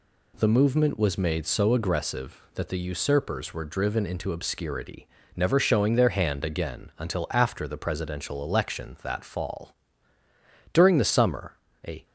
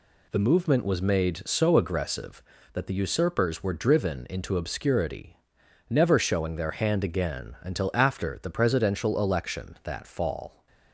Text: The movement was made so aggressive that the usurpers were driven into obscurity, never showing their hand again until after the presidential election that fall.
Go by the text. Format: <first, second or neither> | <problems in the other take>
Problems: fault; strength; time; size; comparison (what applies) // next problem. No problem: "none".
second | goes on to say "During the summer a"; from 10.7 s on; 1.3 s long